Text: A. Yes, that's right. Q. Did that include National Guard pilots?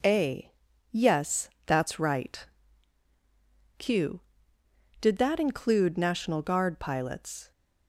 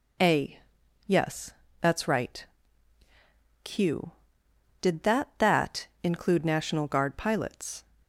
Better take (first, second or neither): first